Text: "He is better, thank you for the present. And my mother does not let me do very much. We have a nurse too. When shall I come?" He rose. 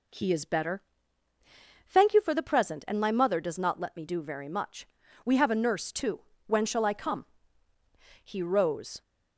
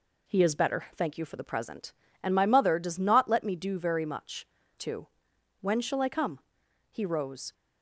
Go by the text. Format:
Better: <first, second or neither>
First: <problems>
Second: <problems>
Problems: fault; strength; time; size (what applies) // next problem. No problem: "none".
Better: first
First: none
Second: skips "We have a nurse"; at 4.6 s